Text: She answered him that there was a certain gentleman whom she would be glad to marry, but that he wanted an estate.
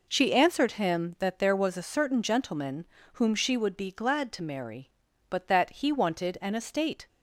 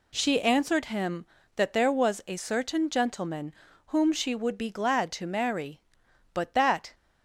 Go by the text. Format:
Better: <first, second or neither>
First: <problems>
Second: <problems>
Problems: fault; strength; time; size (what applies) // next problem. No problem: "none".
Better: first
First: pauses between "gentleman" and "whom"; slight; at 2.8 s; 0.26 s long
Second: pauses between "gentleman" and "whom"; slight; at 3.5 s; 0.32 s long // stops before "he wanted an estate"; at 6.9 s